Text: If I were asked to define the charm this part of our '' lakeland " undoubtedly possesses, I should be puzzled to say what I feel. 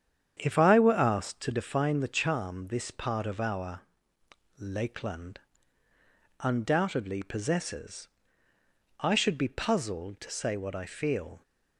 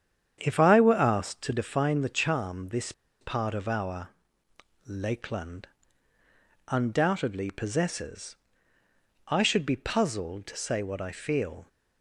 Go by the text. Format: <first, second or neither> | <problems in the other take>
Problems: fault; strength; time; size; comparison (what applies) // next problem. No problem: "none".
first | starts louder than the rest; strong; until 1.4 s; 9 dB; strong in the first // pauses between "this" and "part"; slight; at 2.9 s; 0.27 s long